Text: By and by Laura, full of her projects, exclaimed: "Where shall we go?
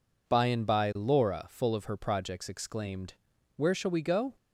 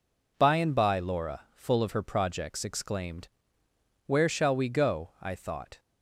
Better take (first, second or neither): first